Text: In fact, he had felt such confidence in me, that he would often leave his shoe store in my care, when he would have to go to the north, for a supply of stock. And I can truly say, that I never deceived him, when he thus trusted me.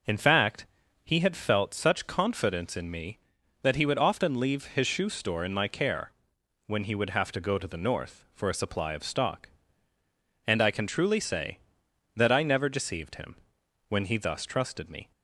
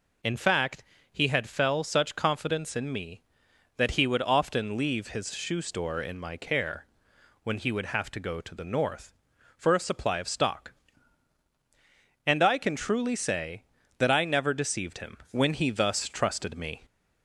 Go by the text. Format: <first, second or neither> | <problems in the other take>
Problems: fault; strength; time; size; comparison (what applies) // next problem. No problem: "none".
first | says "fell" for "felt"; at 1.4 s